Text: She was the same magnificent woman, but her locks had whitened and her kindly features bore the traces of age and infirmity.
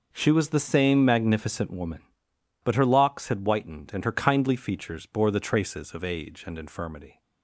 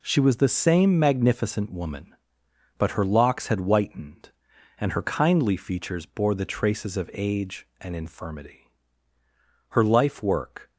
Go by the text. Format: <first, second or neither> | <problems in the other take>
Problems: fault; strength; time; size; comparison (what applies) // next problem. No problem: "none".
first | goes on to say "Her life work"; noticeable; from 9.6 s on; 1.0 s long